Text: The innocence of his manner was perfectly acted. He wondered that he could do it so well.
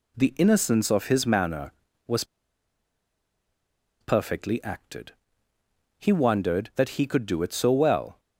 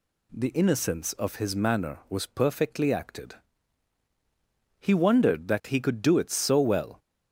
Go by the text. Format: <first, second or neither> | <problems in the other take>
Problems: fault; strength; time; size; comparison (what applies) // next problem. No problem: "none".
second | pauses between "was" and "perfectly"; strong; at 2.2 s; 1.7 s long